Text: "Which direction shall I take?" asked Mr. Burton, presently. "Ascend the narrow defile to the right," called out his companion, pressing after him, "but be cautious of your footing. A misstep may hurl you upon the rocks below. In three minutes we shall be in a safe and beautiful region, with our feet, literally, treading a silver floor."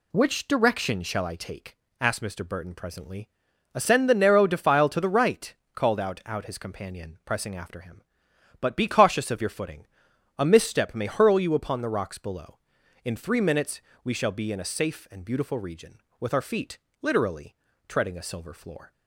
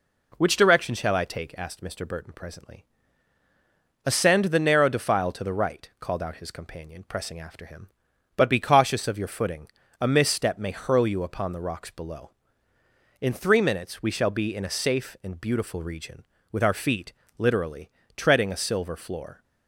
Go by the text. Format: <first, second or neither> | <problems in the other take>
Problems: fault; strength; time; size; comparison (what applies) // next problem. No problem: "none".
second | says "out" twice; at 6.2 s // pauses between "minutes" and "we"; slight; at 13.7 s; 0.24 s long